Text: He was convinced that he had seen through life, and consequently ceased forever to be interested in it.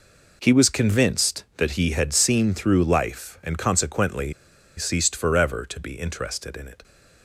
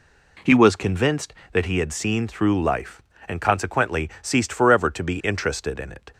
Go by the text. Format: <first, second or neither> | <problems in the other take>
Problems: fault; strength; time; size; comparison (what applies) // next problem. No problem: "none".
second | pauses between "consequently" and "ceased"; at 4.3 s; 0.44 s long